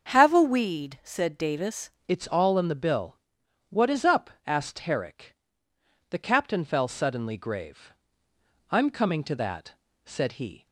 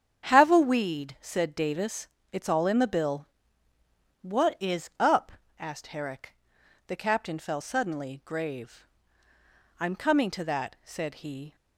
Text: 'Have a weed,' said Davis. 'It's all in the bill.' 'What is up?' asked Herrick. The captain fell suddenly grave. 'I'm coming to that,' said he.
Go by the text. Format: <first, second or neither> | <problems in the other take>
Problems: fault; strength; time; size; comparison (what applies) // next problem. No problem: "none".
second | starts louder than the rest; until 1.1 s; 7 dB; strong in the second // changes voice at "It's"; from 2.0 s on; 8.6 s long